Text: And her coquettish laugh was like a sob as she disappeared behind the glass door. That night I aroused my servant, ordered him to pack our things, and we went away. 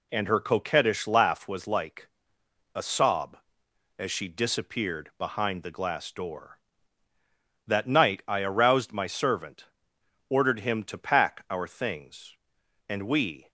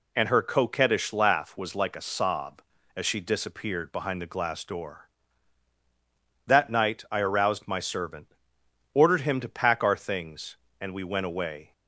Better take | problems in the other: second | pauses between "like" and "a"; noticeable; at 2.0 s; 0.66 s long // stops before "went away"; at 13.4 s

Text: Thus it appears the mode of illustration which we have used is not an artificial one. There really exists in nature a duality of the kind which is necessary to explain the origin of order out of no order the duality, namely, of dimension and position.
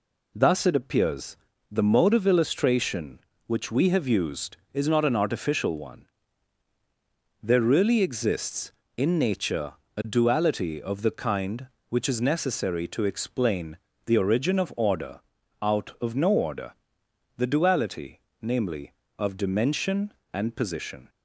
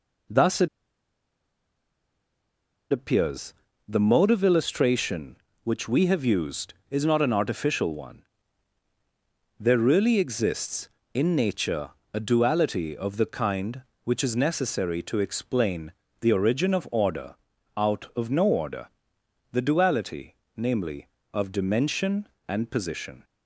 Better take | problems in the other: first | pauses between "it" and "appears"; strong; at 0.6 s; 2.2 s long // pauses between "appears" and "the"; slight; at 3.5 s; 0.34 s long; slight in the first // pauses between "nature" and "a"; slight; at 11.8 s; 0.24 s long; slight in the first // pauses between "explain" and "the"; slight; at 15.9 s; 0.30 s long; slight in the first // pauses between "order" and "out"; at 17.3 s; 0.40 s long; also in the first // pauses between "order" and "the"; noticeable; at 18.8 s; 0.64 s long; noticeable in the first

